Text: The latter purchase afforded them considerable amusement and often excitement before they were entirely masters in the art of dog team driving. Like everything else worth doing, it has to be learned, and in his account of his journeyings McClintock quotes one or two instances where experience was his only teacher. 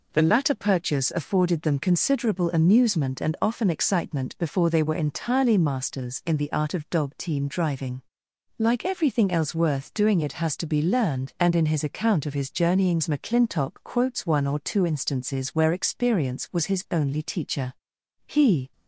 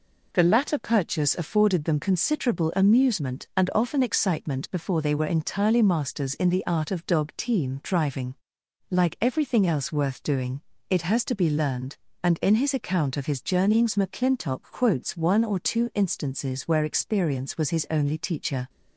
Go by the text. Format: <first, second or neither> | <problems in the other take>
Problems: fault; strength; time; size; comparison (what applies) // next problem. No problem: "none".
second | goes on to say "He"; slight; from 18.2 s on; 0.46 s long